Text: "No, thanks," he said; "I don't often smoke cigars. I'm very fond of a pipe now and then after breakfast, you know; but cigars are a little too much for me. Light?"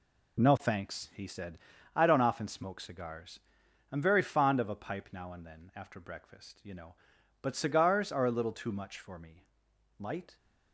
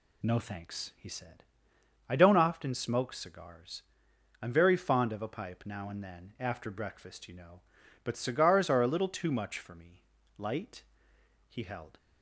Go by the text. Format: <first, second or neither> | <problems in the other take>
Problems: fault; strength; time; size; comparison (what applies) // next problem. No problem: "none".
first | goes on to say "He held"; slight; from 11.4 s on; 0.48 s long